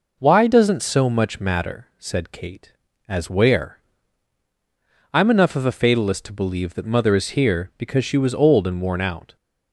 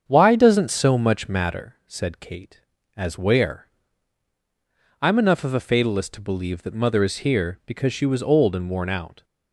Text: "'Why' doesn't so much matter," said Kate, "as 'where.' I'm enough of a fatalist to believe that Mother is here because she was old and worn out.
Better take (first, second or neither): first